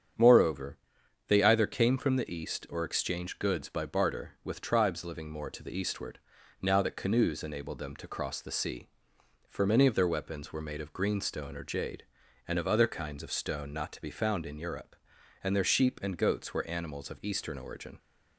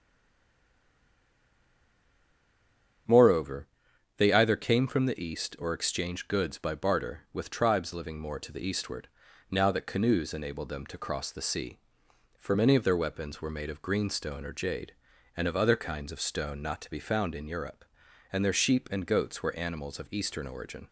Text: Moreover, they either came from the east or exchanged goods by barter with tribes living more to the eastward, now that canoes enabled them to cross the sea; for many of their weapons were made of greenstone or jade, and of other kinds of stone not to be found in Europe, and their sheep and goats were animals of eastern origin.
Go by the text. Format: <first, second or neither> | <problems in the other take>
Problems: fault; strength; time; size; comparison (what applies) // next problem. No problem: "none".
first | stays silent before the first word; strong; until 3.0 s; 3.0 s long // starts louder than the rest; strong; until 4.5 s; 8 dB; strong in the first